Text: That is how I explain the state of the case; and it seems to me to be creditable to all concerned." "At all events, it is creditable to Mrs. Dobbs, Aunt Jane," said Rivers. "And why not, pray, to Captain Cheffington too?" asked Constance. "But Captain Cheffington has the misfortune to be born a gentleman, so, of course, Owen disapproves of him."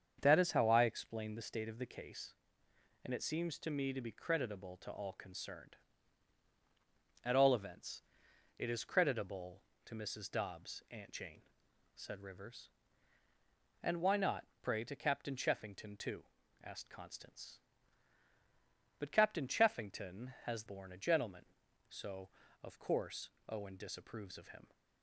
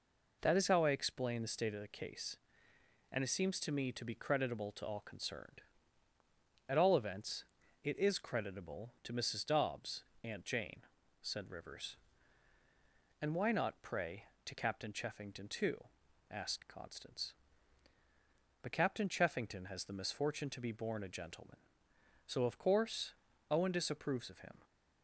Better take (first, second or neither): second